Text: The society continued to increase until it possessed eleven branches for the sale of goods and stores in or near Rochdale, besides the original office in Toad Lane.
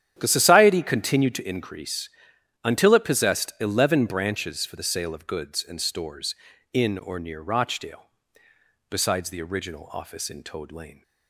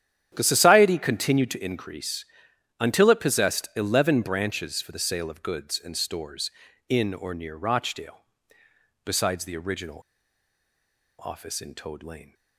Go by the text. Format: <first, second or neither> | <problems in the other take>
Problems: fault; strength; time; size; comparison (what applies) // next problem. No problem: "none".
first | starts louder than the rest; strong; until 1.3 s; 10 dB; strong in the first // pauses between "increase" and "until"; noticeable; at 2.2 s; 0.54 s long; noticeable in the first // pauses between "original" and "office"; at 10.0 s; 1.2 s long